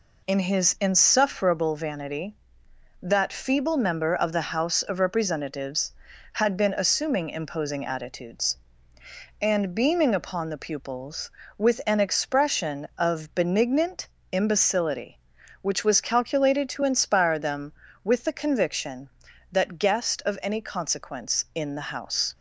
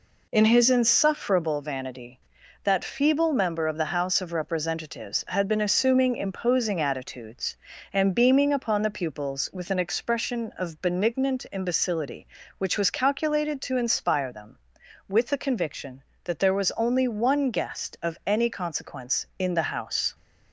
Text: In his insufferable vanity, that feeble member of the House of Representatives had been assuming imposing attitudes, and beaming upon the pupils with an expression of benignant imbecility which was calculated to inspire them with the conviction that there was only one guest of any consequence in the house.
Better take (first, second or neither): second